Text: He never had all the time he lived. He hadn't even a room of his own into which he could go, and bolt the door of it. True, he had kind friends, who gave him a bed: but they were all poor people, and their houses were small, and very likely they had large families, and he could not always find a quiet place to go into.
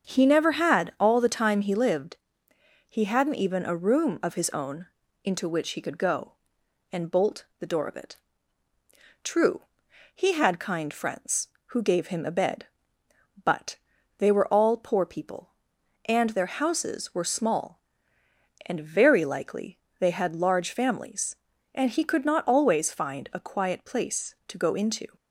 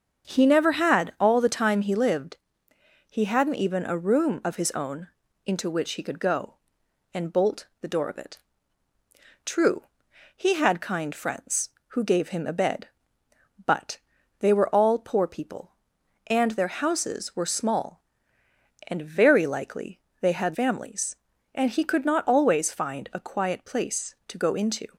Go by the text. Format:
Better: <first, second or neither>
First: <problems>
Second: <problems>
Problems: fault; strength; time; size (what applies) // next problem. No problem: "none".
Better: first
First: starts louder than the rest; until 1.1 s; 7 dB // pauses between "own" and "into"; at 4.8 s; 0.38 s long // pauses between "but" and "they"; at 13.7 s; 0.40 s long // pauses between "likely" and "they"; slight; at 19.7 s; 0.22 s long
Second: starts louder than the rest; until 1.3 s; 7 dB // pauses between "own" and "into"; at 5.0 s; 0.38 s long // pauses between "but" and "they"; at 13.9 s; 0.40 s long // pauses between "likely" and "they"; slight; at 19.9 s; 0.22 s long // skips "large"; at 20.5 s